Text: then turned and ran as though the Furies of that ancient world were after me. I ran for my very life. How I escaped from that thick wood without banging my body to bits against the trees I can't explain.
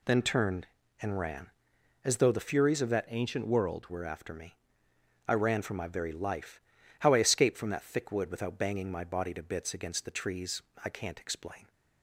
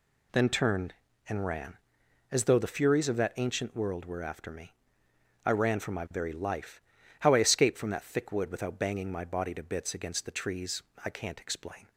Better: second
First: changes voice from "ancient" to "world"; from 3.0 to 3.8 s; 0.8 s long // pauses between "trees" and "I"; slight; at 10.5 s; 0.24 s long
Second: pauses between "trees" and "I"; slight; at 10.8 s; 0.24 s long

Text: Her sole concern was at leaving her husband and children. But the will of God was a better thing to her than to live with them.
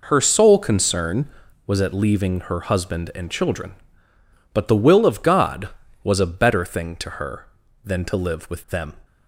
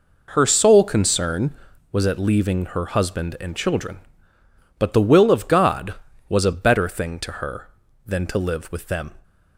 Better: neither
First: none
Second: none

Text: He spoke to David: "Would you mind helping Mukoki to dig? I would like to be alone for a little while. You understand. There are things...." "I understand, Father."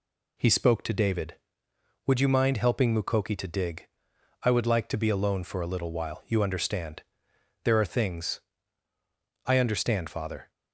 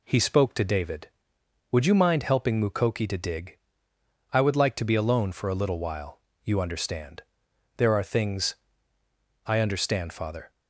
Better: neither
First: none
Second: none

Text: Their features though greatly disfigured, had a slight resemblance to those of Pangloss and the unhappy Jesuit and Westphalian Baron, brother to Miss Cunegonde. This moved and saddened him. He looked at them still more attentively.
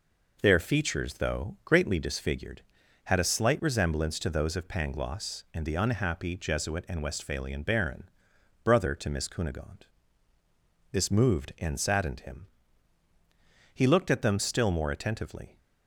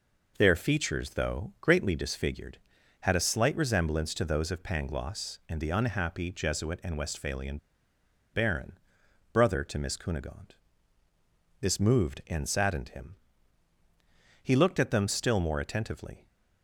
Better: first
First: none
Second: pauses between "Westphalian" and "Baron"; noticeable; at 7.5 s; 0.76 s long

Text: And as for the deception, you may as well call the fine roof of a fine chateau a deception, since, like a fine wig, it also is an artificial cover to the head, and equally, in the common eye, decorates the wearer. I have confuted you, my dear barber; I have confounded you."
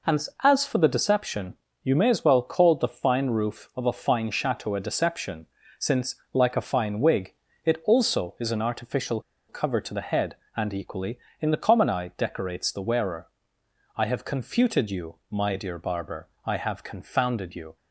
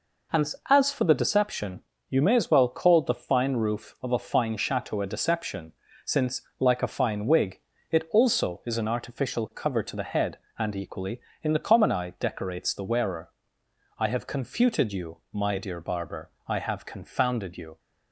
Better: second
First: pauses between "artificial" and "cover"; slight; at 9.2 s; 0.28 s long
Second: none

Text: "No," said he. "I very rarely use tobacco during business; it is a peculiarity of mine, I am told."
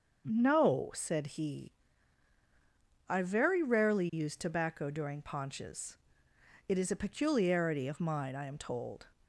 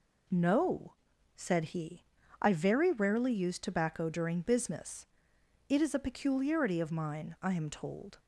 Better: second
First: starts louder than the rest; until 1.4 s; 6.5 dB // says "paunches" for "business"; at 5.2 s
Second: none

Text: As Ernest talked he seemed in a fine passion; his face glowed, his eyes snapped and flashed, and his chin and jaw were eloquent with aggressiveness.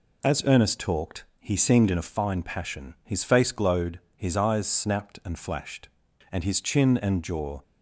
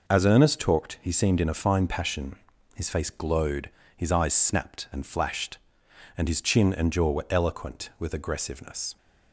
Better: second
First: pauses between "talked" and "he"; slight; at 1.2 s; 0.16 s long // stops before "were eloquent with aggressiveness"; at 7.6 s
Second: none

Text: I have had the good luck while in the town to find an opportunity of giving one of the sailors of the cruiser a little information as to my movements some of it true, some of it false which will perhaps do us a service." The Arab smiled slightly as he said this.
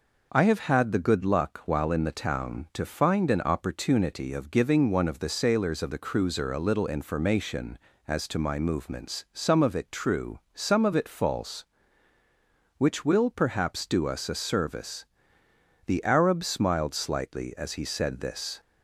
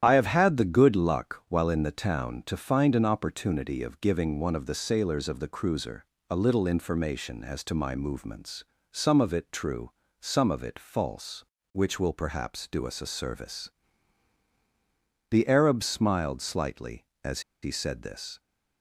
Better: first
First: none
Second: starts louder than the rest; strong; until 1.0 s; 10.5 dB // pauses between "cruiser" and "a"; slight; at 6.0 s; 0.26 s long // pauses between "movements" and "some"; slight; at 8.6 s; 0.26 s long // pauses between "as" and "he"; slight; at 17.3 s; 0.22 s long

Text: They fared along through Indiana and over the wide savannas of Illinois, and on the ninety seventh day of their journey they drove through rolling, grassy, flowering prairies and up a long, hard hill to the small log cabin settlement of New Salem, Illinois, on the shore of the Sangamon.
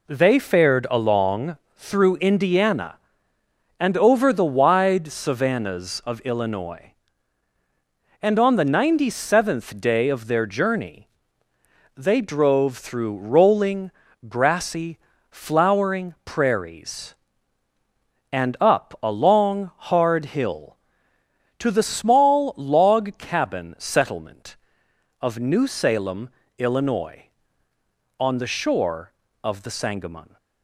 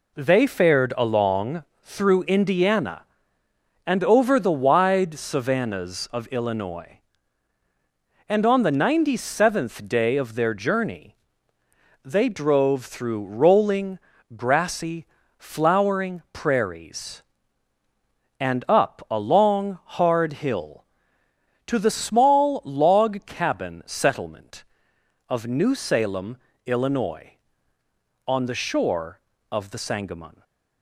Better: neither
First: pauses between "along" and "through"; slight; at 1.5 s; 0.20 s long // pauses between "journey" and "they"; noticeable; at 11.0 s; 0.88 s long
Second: pauses between "along" and "through"; slight; at 1.6 s; 0.20 s long // pauses between "journey" and "they"; noticeable; at 11.1 s; 0.88 s long

